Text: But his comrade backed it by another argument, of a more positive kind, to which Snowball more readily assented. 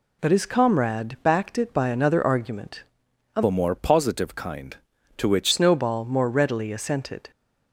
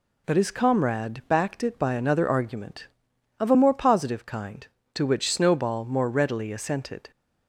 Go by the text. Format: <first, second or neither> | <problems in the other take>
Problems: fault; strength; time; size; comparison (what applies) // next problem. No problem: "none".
second | changes voice from "a" to "which"; from 3.4 to 5.5 s; 2.1 s long